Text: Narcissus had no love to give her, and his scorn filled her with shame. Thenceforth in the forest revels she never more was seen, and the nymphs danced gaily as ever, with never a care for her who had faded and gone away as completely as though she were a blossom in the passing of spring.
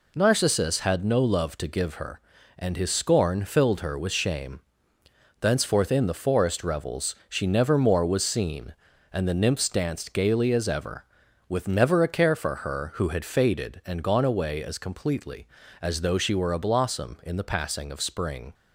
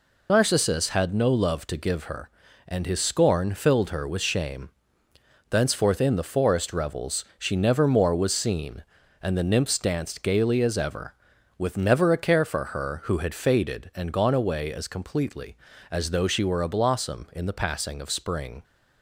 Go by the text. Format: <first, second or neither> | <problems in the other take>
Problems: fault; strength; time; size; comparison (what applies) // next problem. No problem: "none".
first | loses the start of "Narcissus"; at 0.2 s; 50 ms // pauses between "revels" and "she"; slight; at 7.2 s; 0.16 s long; slight in the first